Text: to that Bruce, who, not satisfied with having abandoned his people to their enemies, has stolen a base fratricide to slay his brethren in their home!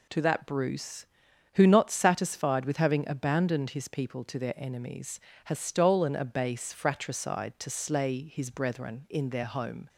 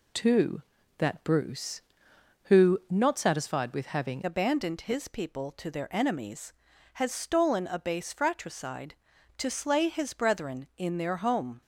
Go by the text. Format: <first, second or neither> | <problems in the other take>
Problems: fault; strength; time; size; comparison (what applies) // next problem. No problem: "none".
first | changes voice at "abandoned"; from 4.2 s on; 7.4 s long